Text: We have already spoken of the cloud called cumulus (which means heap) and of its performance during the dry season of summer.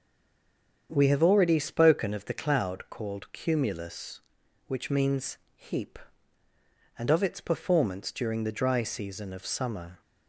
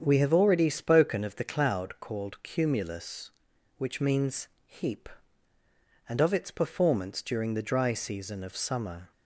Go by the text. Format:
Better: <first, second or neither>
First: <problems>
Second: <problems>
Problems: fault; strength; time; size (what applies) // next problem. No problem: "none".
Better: second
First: stays silent before the first word; slight; until 0.8 s; 0.8 s long // starts louder than the rest; strong; until 1.9 s; 8 dB // pauses between "means" and "heap"; slight; at 5.3 s; 0.18 s long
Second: starts louder than the rest; strong; until 1.0 s; 8 dB // pauses between "means" and "heap"; slight; at 4.4 s; 0.18 s long